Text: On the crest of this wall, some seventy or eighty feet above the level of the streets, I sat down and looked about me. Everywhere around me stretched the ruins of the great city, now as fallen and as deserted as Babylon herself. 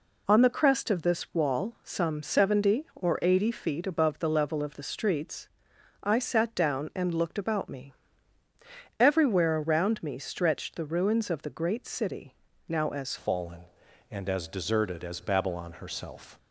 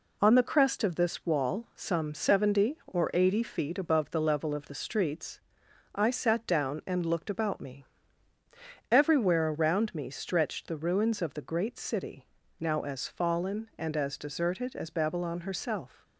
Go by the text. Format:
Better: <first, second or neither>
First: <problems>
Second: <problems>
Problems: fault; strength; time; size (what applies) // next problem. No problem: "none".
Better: second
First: changes voice at "fallen"; from 13.1 s on; 3.2 s long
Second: none